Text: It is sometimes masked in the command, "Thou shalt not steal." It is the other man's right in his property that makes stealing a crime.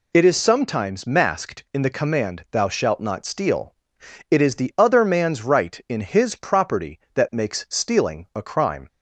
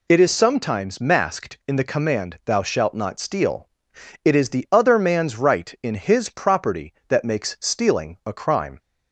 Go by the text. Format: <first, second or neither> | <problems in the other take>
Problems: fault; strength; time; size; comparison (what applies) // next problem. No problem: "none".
neither | none